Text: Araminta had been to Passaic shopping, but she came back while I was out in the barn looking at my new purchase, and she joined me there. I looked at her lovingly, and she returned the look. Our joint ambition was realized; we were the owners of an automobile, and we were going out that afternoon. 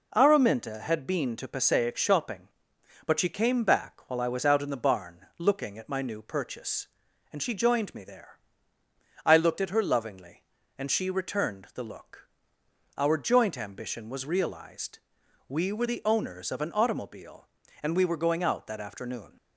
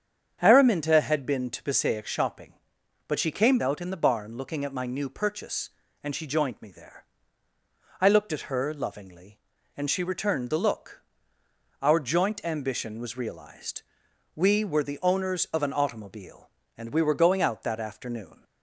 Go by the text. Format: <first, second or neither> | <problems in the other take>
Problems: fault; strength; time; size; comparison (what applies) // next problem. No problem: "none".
first | starts louder than the rest; strong; until 1.4 s; 8 dB // skips "back while I was"; at 3.5 s